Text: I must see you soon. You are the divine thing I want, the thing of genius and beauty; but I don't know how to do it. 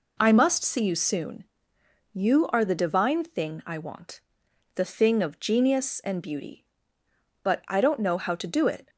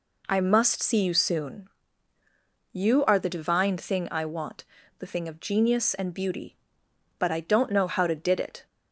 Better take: first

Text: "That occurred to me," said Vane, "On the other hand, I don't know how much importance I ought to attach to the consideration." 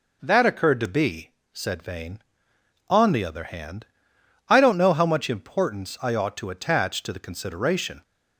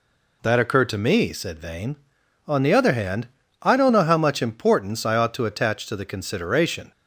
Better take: second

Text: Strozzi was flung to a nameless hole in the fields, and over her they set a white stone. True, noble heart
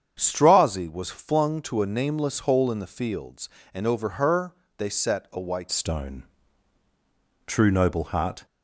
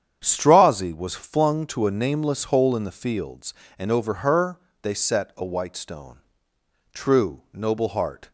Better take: second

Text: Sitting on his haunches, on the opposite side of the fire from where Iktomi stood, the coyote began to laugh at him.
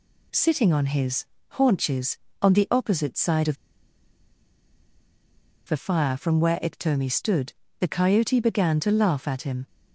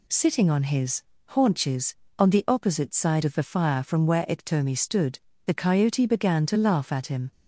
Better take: second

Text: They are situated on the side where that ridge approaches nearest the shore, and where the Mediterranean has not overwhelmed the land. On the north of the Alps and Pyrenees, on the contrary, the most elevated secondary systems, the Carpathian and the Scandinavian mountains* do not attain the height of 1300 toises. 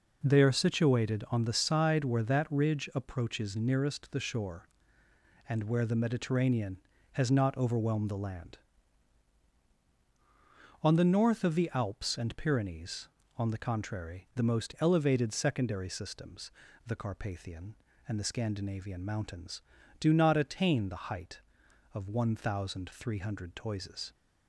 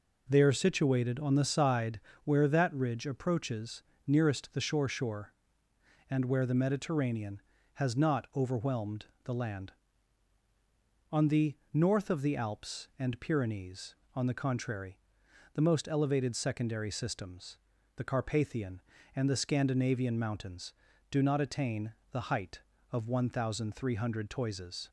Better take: first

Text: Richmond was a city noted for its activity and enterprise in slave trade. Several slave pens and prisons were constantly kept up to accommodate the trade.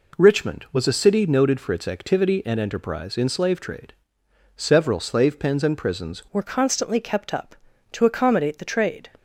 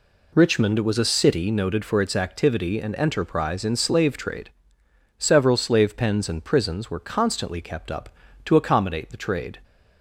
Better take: second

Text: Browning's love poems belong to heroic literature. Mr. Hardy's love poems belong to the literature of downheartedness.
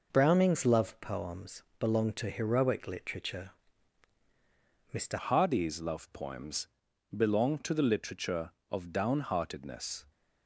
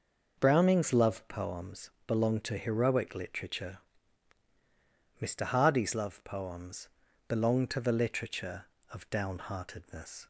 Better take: second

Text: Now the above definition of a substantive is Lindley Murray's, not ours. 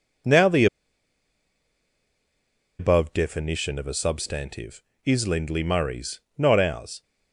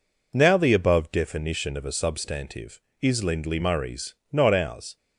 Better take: second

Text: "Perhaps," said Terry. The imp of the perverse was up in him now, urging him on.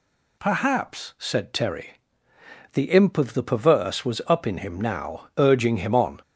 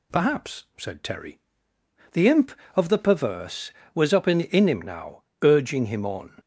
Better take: first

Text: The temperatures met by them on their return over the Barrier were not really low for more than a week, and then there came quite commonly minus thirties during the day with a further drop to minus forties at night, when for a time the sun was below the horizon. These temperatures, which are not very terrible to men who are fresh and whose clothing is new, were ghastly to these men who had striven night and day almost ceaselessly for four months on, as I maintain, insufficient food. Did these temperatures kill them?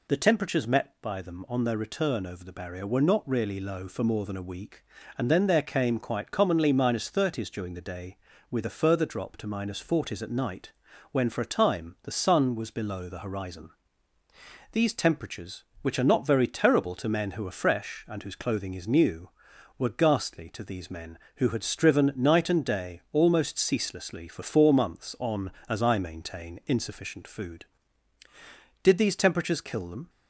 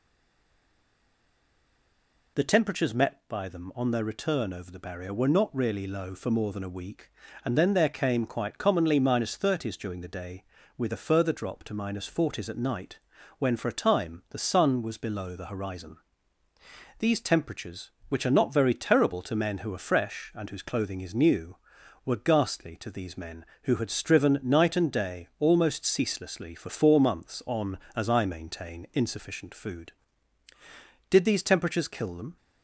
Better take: first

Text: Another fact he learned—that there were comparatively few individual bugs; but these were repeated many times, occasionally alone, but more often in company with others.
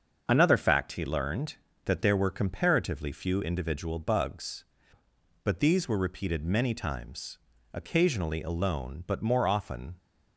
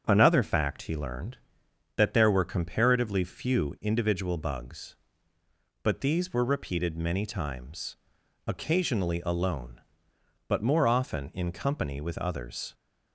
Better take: second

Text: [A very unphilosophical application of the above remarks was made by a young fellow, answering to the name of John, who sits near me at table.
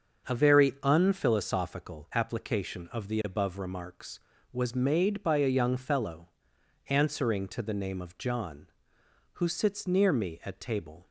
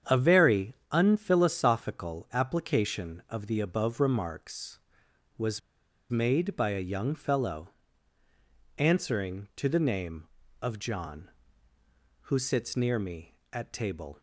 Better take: first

